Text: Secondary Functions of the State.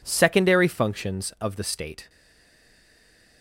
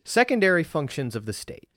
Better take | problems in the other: second | stays silent after the last word; noticeable; from 2.0 s on; 1.4 s long

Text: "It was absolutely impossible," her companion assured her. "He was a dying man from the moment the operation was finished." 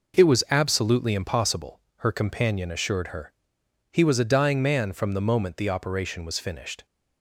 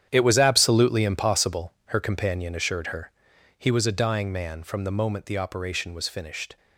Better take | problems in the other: first | gets quieter; strong; throughout; 13 dB

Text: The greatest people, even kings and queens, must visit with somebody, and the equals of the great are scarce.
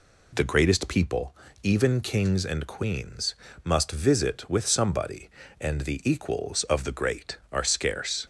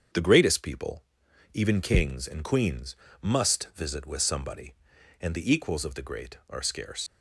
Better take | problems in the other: first | starts louder than the rest; strong; until 1.6 s; 7.5 dB // leaves "scarce" unfinished; at 7.0 s; 70 ms

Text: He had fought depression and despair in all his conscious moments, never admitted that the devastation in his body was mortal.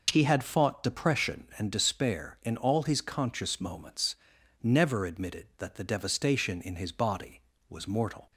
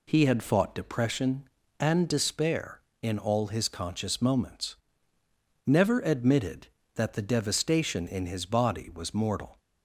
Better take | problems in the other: neither | none

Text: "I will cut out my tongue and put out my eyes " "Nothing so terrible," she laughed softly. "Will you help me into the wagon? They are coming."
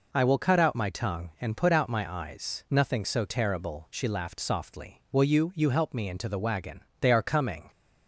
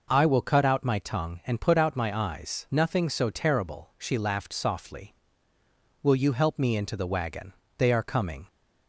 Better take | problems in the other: second | says "you" twice; at 5.5 s

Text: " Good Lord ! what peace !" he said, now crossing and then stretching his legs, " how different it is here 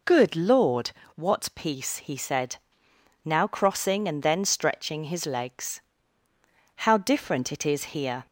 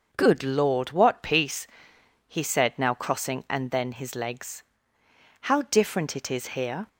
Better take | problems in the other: first | starts louder than the rest; until 1.1 s; 6.5 dB // skips "stretching"; at 3.9 s

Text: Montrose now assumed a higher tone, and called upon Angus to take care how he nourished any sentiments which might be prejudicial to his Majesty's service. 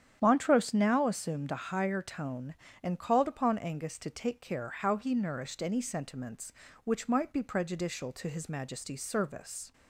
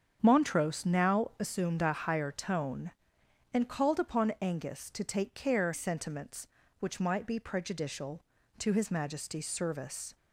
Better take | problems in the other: first | starts louder than the rest; strong; until 1.2 s; 8 dB; strong in the first // skips "how he nourished any"; at 5.7 s

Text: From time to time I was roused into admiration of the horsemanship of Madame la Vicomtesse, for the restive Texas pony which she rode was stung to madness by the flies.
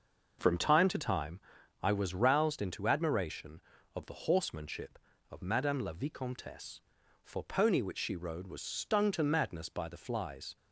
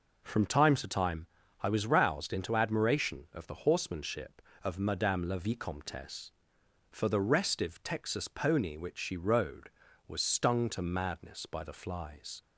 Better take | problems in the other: second | pauses between "time" and "I"; at 1.3 s; 0.44 s long; slight in the second // skips "the restive Texas"; at 7.4 s

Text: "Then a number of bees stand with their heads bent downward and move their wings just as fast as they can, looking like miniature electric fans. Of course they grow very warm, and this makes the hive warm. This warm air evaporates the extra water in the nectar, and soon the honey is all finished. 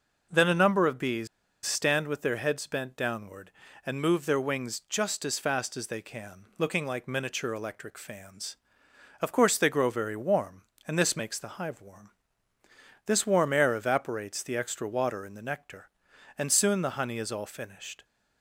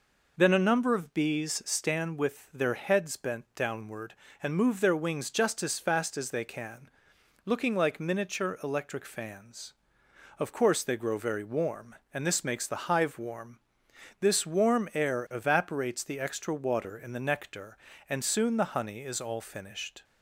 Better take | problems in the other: second | pauses between "bees" and "stand"; at 1.2 s; 0.38 s long

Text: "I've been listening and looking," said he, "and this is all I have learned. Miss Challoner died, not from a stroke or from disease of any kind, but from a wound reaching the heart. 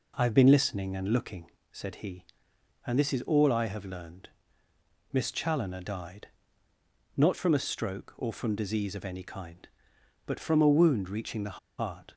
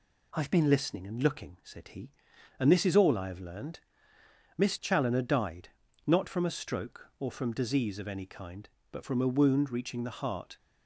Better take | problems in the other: second | pauses between "the" and "heart"; slight; at 11.5 s; 0.19 s long

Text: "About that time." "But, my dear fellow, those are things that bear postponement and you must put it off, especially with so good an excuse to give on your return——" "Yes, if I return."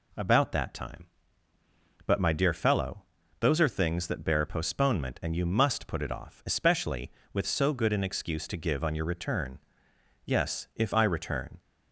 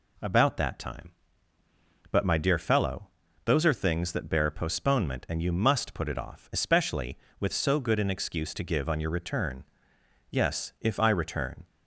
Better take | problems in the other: neither | none

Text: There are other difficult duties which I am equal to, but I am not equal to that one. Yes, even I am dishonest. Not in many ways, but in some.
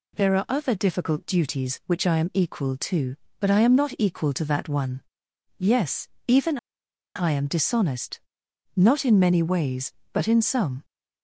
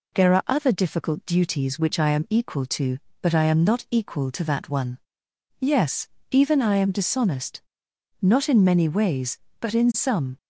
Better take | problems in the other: second | pauses between "even" and "I"; noticeable; at 6.5 s; 0.59 s long

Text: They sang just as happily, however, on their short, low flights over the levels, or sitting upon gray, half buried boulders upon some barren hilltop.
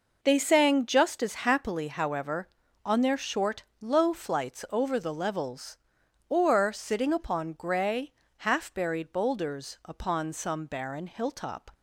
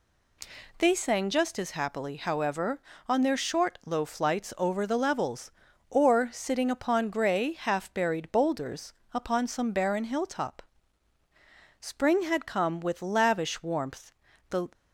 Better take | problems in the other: first | pauses between "boulders" and "upon"; slight; at 8.9 s; 0.20 s long // goes on to say "Spring had come with lavish warmth The"; strong; from 11.7 s on; 2.9 s long

